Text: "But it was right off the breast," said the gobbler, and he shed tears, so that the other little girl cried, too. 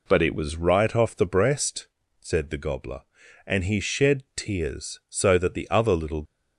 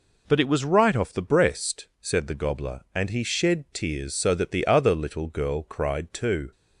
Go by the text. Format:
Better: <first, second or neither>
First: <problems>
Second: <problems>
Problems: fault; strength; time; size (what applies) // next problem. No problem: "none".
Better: second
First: stops before "girl cried too"; at 6.2 s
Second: none